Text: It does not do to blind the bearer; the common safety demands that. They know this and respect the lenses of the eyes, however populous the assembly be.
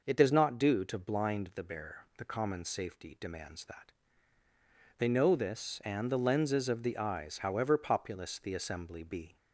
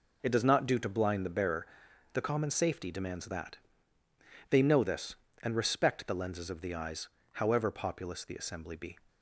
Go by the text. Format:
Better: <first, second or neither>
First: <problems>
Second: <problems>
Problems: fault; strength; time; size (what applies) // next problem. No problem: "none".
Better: second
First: skips "respect"; at 6.1 s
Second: none